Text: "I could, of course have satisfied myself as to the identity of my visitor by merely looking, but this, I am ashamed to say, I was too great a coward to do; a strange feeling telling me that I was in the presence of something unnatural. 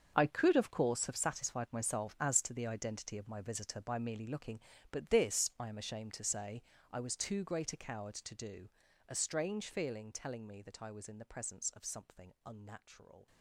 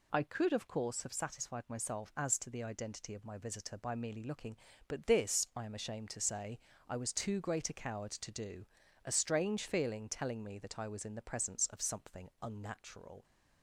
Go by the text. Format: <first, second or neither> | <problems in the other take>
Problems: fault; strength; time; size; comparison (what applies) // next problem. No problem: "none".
second | gets quieter; strong; throughout; 14.5 dB